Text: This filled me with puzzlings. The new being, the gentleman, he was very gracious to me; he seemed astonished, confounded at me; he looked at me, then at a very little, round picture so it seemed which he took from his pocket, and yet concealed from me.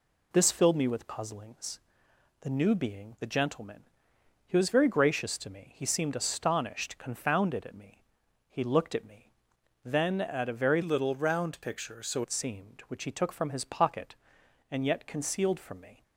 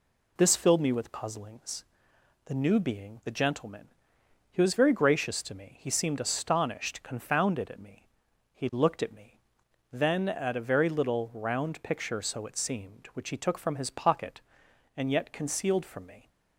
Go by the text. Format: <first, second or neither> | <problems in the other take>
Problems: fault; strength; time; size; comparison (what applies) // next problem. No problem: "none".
second | changes voice from "little" to "so"; from 10.8 to 12.2 s; 1.4 s long